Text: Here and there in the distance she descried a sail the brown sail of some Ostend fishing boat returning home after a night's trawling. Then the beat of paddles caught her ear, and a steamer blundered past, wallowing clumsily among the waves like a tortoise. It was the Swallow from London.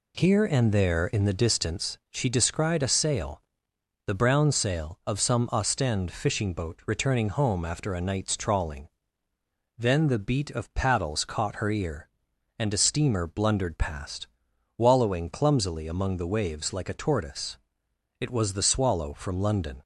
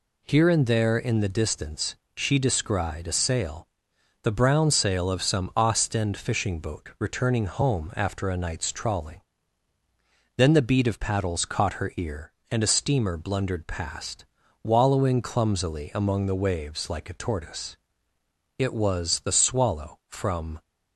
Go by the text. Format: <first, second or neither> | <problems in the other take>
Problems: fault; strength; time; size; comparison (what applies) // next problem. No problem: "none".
first | pauses between "distance" and "she"; slight; at 1.9 s; 0.20 s long // pauses between "sail" and "the"; noticeable; at 3.6 s; 0.56 s long; noticeable in the first // stops before "London"; at 20.6 s